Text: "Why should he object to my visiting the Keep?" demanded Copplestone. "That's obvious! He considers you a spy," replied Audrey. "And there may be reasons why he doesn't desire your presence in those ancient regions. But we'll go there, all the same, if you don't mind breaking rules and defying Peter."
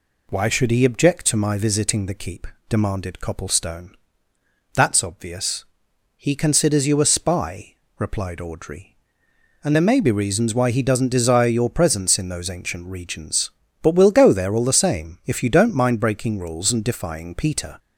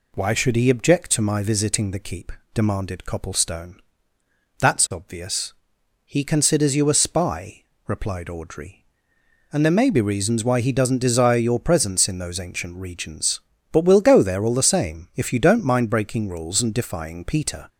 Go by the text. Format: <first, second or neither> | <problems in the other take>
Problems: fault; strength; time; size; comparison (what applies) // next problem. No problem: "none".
neither | none